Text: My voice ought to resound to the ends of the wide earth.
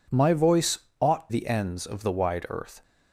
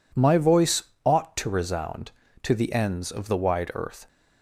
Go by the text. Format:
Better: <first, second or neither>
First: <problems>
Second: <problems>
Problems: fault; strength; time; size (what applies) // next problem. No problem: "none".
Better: second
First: pauses between "voice" and "ought"; slight; at 0.7 s; 0.22 s long // skips "to resound to"; at 1.3 s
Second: pauses between "voice" and "ought"; slight; at 0.8 s; 0.22 s long